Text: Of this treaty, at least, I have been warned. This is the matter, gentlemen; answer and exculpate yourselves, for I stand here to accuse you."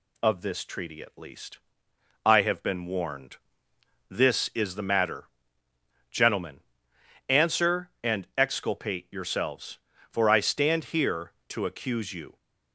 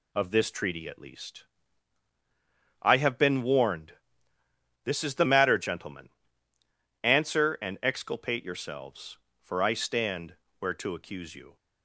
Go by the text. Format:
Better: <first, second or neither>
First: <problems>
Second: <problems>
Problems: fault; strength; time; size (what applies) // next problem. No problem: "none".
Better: first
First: none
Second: says "where" for "here"; at 10.5 s